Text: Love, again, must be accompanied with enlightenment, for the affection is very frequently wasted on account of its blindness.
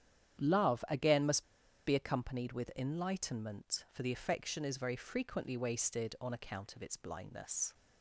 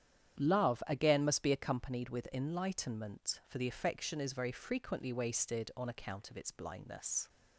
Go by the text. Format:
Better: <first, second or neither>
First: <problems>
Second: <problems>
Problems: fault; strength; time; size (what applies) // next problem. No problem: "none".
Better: second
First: starts louder than the rest; strong; until 1.8 s; 9.5 dB // pauses between "must" and "be"; at 1.4 s; 0.43 s long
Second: starts louder than the rest; strong; until 1.4 s; 9.5 dB